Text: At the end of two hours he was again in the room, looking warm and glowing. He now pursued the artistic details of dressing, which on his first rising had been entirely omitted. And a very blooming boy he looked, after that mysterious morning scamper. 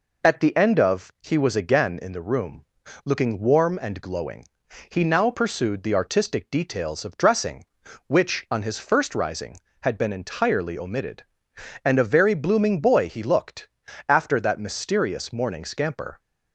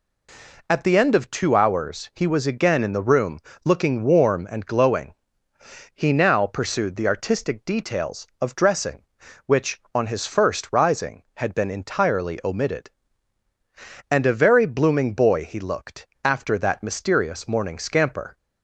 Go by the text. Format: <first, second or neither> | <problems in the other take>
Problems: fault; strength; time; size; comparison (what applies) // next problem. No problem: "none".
second | skips "two hours"; at 1.1 s